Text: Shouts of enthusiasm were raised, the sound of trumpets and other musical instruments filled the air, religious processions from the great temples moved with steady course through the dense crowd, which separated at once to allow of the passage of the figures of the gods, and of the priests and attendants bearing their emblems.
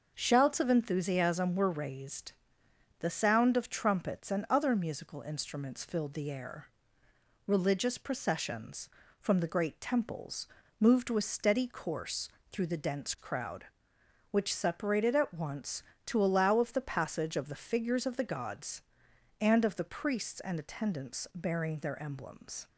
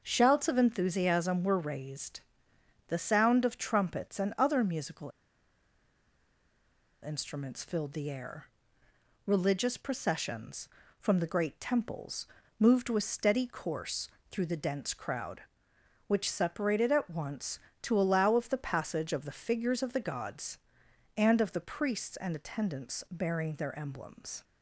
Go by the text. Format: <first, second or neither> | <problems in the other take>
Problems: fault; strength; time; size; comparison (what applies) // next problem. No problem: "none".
first | pauses between "musical" and "instruments"; strong; at 5.1 s; 1.9 s long // pauses between "temples" and "moved"; slight; at 12.2 s; 0.32 s long; slight in the first // pauses between "course" and "through"; slight; at 14.0 s; 0.24 s long; slight in the first